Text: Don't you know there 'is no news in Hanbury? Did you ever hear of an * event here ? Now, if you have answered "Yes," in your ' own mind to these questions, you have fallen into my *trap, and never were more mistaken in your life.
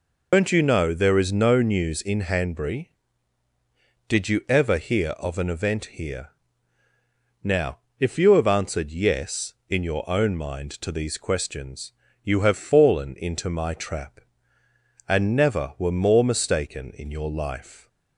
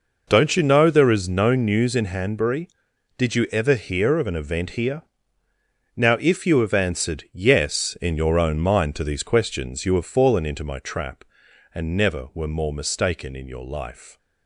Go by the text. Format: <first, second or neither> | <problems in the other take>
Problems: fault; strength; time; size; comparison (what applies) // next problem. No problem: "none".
second | loses the start of "Don't"; at 0.3 s; 70 ms